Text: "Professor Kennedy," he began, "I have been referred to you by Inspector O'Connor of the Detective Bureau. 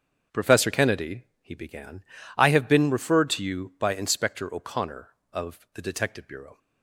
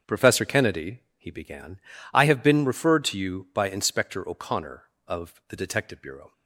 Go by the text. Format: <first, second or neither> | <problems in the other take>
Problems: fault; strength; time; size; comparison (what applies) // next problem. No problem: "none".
neither | starts louder than the rest; the same in both